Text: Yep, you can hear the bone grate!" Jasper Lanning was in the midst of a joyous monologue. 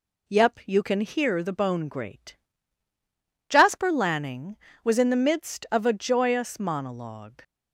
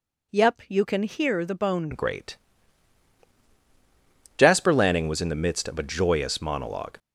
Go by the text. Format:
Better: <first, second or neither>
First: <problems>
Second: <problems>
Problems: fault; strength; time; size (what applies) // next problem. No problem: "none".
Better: first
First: none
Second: changes voice at "grate"; from 1.9 s on; 5.0 s long